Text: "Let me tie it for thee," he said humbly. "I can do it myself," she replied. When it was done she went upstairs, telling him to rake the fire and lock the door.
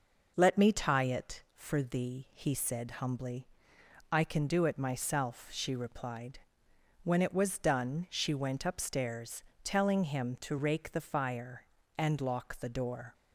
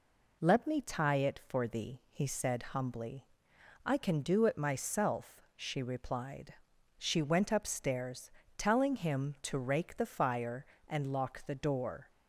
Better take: first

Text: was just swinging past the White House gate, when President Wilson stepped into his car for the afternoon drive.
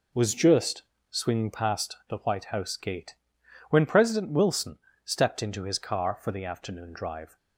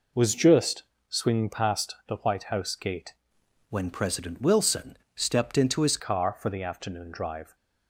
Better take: first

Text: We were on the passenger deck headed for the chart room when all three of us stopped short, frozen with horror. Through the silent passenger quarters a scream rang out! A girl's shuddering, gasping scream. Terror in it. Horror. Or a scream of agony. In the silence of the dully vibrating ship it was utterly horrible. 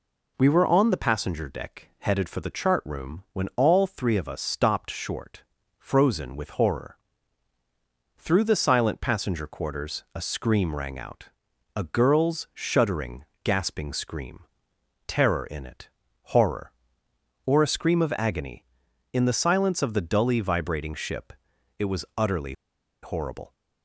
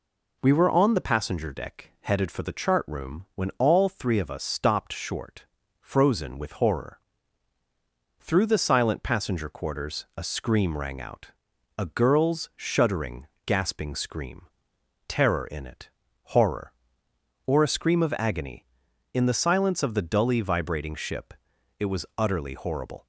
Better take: second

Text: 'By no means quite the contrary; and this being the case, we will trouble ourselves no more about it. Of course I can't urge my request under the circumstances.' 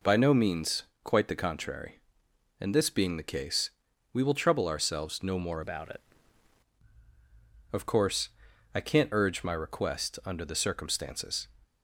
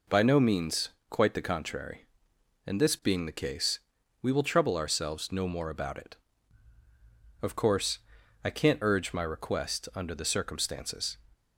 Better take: second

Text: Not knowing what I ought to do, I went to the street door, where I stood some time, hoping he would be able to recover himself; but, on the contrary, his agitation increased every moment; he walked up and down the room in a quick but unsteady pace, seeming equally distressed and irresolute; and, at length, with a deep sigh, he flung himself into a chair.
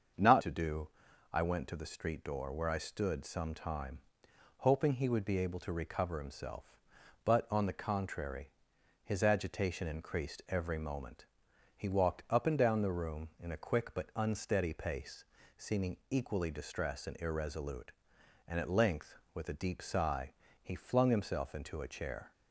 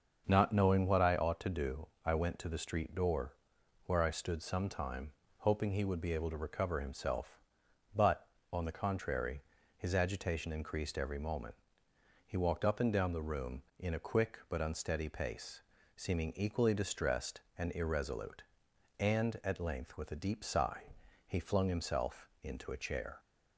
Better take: second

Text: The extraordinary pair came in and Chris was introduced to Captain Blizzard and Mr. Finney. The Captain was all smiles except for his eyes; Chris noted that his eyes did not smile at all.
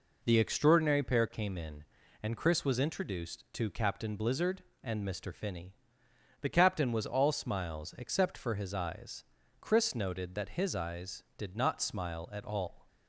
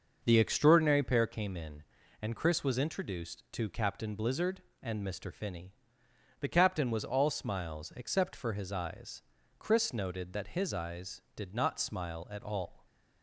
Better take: first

